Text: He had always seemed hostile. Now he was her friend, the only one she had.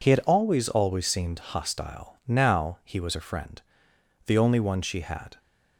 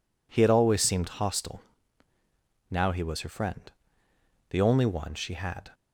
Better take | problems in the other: second | says "always" twice; at 0.6 s

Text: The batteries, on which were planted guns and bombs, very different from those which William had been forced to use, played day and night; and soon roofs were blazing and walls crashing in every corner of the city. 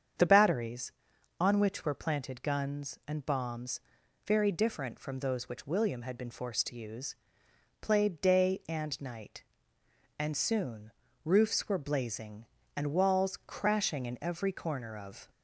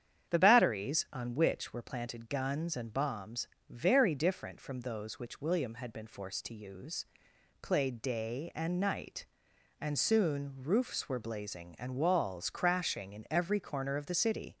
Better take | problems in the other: second | starts louder than the rest; strong; until 1.6 s; 7.5 dB; strong in the second // pauses between "soon" and "roofs"; slight; at 10.8 s; 0.34 s long // stops before "the city"; at 15.2 s

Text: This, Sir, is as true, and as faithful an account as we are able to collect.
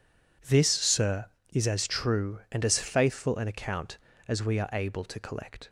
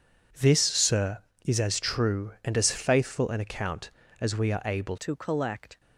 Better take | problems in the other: first | changes voice at "to"; from 4.9 s on; 0.8 s long

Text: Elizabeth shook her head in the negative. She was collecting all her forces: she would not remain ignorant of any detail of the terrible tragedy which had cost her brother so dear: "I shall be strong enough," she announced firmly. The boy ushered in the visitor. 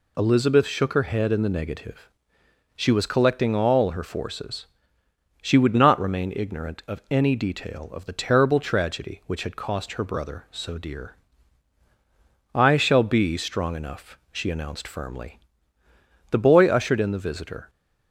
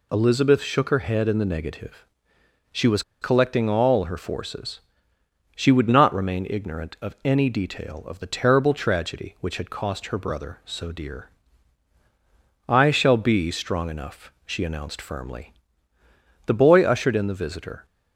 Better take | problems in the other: first | pauses between "was" and "collecting"; slight; at 3.0 s; 0.20 s long

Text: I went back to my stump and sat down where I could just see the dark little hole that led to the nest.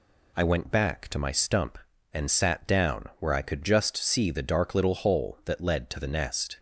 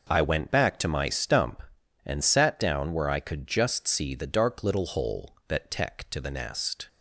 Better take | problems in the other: first | says "tech" for "led"; at 5.6 s

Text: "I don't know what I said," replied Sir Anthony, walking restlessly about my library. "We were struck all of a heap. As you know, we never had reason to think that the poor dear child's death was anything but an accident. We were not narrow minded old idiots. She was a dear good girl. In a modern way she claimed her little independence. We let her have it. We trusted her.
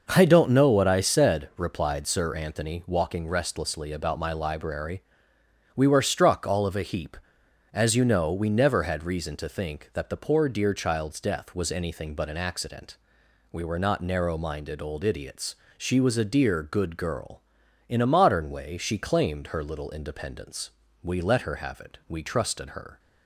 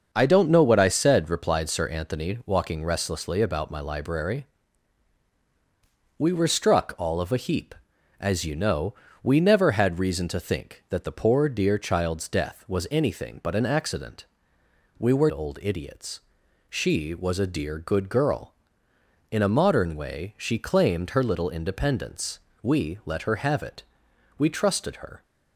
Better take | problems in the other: first | starts louder than the rest; until 1.1 s; 6.5 dB // skips "not narrow minded"; at 15.3 s

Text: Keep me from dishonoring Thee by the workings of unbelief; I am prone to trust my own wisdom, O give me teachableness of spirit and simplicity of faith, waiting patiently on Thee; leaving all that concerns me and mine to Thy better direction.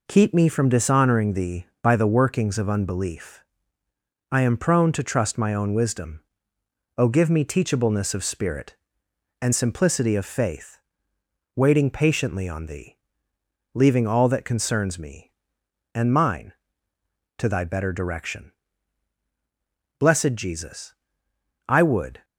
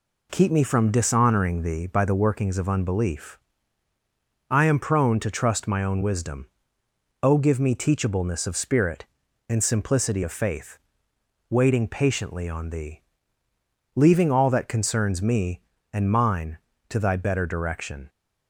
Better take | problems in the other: second | goes on to say "Blessed Jesus I would"; strong; from 19.9 s on; 2.2 s long

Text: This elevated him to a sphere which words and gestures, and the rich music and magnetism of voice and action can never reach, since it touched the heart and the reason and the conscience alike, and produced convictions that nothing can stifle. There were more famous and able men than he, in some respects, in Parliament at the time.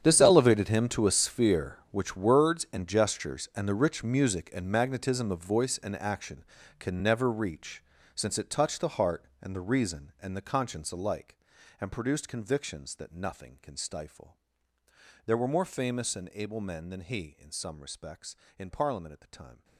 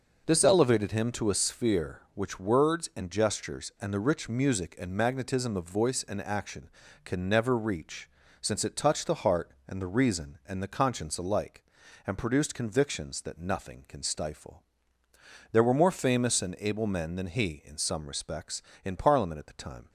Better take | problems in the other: second | gets quieter; strong; throughout; 17.5 dB

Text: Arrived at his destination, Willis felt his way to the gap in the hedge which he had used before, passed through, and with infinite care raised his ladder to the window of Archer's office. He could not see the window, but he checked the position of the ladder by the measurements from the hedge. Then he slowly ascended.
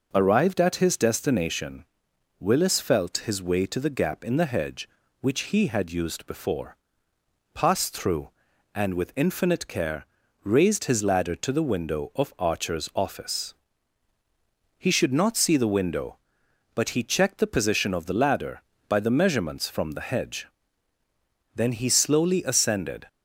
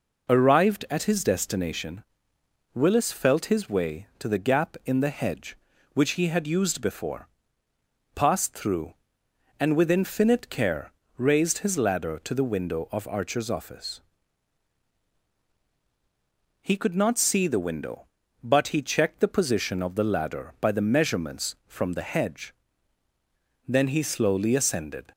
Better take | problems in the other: second | pauses between "care" and "raised"; at 10.0 s; 0.38 s long; slight in the second // says "should" for "could"; at 14.8 s

